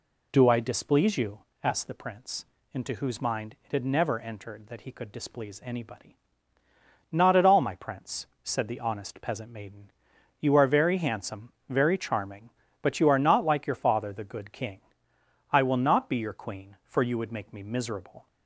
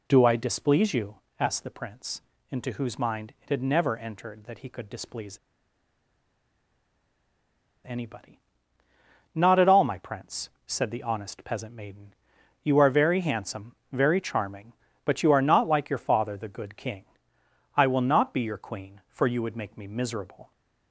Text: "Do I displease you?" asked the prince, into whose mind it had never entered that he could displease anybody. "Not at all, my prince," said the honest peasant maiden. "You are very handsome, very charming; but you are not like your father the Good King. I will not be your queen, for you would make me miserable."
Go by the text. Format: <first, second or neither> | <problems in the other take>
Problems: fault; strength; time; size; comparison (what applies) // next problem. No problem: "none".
first | pauses between "displease" and "anybody"; strong; at 5.3 s; 2.4 s long